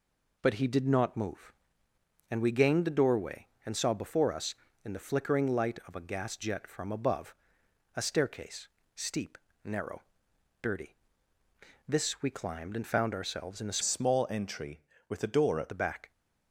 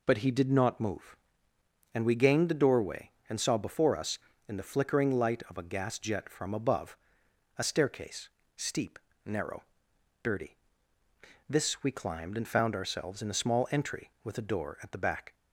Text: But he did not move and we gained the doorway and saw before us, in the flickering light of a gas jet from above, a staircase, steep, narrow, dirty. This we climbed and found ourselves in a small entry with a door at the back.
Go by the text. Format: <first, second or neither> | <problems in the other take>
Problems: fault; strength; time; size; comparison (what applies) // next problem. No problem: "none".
second | changes voice from "small" to "at"; from 13.8 to 15.6 s; 1.8 s long